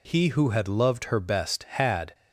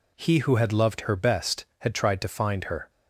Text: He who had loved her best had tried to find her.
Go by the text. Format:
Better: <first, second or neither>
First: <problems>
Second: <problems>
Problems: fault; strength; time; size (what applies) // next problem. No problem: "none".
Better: second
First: stops before "tried to find her"; at 2.1 s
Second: none